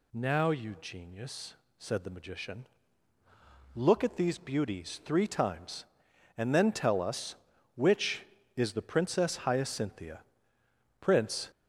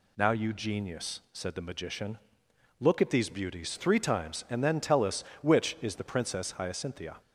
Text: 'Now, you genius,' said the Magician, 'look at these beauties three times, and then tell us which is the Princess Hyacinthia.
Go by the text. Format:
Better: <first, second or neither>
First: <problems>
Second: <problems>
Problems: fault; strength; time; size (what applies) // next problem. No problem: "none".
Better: second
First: goes on to say "Prince"; from 11.0 s on; 0.50 s long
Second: none